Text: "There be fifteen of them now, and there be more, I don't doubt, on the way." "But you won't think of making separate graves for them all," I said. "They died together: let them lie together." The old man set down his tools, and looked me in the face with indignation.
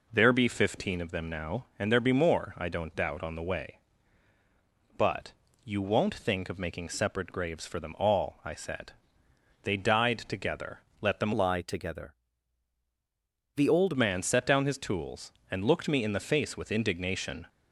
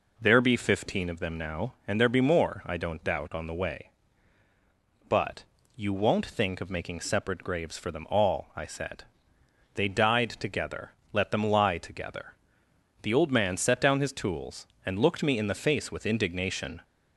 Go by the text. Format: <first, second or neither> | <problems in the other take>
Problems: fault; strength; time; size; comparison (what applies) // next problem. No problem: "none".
second | pauses between "But" and "you"; slight; at 5.3 s; 0.30 s long; slight in the second // changes voice from "lie" to "old"; from 11.3 to 13.9 s; 2.6 s long